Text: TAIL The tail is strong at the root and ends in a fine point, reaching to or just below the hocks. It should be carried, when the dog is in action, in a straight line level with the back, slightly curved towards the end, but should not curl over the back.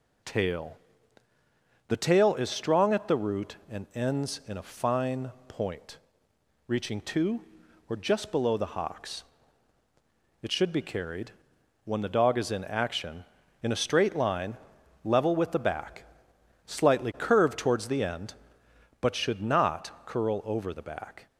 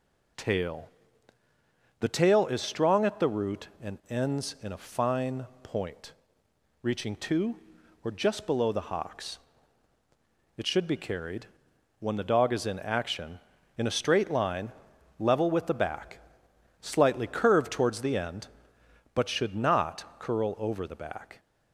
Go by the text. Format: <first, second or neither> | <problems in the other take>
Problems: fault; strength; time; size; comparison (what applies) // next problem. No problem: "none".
neither | pauses between "TAIL" and "The"; the same in both // pauses between "fine" and "point"; slight; the same in both // pauses between "line" and "level"; noticeable; the same in both // pauses between "not" and "curl"; slight; the same in both